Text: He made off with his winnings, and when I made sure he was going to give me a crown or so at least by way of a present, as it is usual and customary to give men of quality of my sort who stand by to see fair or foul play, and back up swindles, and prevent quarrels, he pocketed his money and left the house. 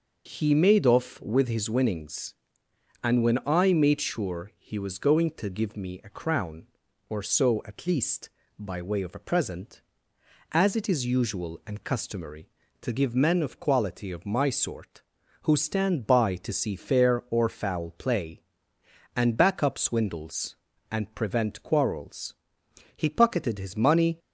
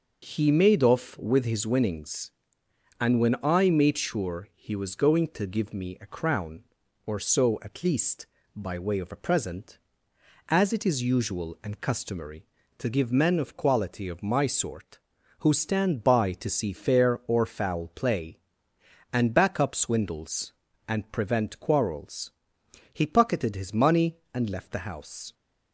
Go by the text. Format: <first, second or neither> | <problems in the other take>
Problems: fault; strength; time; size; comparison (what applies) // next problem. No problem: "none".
second | stops before "and left the house"; at 24.1 s